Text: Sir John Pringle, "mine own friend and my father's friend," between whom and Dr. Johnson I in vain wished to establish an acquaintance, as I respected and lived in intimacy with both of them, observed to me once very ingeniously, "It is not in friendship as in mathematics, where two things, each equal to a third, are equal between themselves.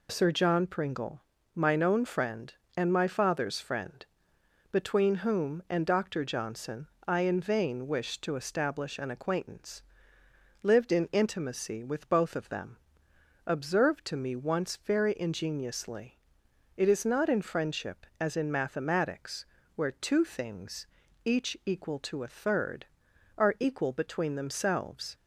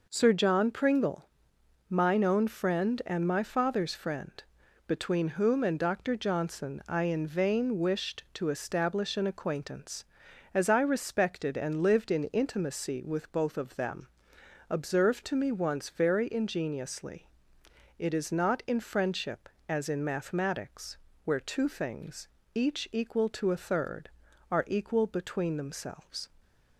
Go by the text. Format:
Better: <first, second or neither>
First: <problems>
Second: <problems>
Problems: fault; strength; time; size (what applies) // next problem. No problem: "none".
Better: second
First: pauses between "Johnson" and "I"; slight; at 6.8 s; 0.18 s long // skips "as I respected and"; at 10.2 s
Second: none